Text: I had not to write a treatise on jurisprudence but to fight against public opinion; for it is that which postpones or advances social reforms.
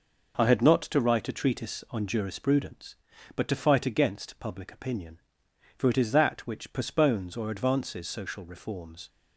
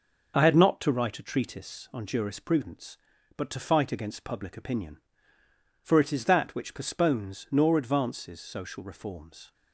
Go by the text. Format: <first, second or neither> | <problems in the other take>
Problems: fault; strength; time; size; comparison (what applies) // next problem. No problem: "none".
first | says "nor" for "or"; at 7.5 s